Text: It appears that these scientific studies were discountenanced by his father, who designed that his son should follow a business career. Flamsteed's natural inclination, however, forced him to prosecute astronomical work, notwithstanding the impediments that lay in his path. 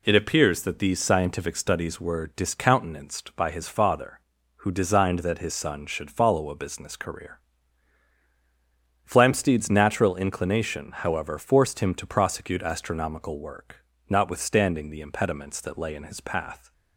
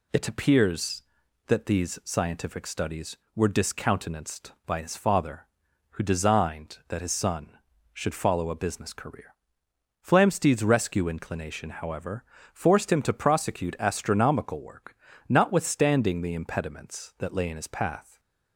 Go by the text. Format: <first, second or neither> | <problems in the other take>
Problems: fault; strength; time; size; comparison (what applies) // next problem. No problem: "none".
first | says "rescue" for "natural"; at 10.6 s